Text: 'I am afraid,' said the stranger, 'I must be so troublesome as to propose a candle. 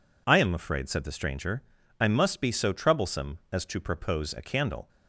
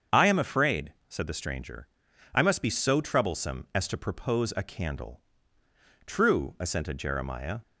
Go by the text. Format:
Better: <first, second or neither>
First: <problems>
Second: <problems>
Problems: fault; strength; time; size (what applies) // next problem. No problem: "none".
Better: first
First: none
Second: starts louder than the rest; strong; until 1.2 s; 7.5 dB // goes on to say "True assented Jeremiah"; from 6.0 s on; 1.5 s long